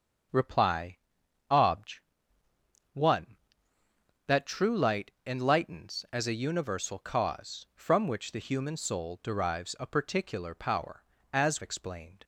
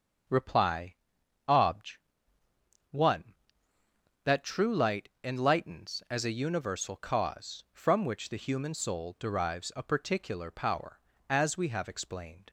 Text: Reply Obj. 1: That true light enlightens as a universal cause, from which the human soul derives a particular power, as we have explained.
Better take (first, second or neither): second